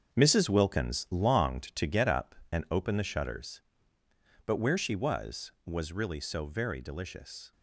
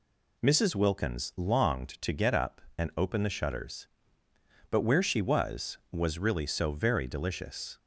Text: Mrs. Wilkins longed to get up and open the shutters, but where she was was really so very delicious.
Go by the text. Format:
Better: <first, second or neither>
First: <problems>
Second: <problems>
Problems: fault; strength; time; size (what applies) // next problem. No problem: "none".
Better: second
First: gets quieter; strong; throughout; 8.5 dB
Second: none